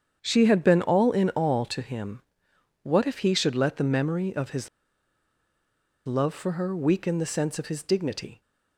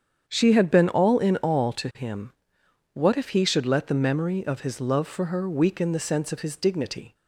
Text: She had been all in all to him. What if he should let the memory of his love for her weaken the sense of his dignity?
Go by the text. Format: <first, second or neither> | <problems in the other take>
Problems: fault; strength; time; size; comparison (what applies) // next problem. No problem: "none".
second | starts louder than the rest; strong; until 1.2 s; 7.5 dB; strong in the second // pauses between "his" and "love"; strong; at 4.6 s; 1.3 s long